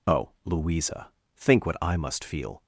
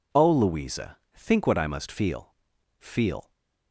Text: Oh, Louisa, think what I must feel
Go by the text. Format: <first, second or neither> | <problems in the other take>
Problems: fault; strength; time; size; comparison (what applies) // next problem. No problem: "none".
first | says "feel" twice; at 2.7 s